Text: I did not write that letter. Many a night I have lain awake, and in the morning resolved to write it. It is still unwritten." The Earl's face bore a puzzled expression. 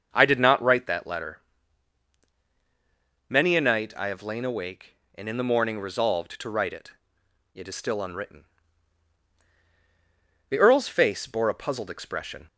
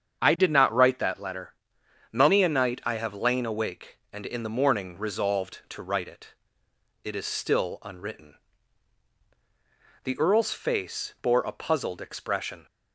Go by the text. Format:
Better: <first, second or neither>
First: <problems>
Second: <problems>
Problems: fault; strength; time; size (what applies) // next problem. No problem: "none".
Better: neither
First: starts louder than the rest; until 1.1 s; 6.5 dB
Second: starts louder than the rest; strong; until 1.2 s; 7.5 dB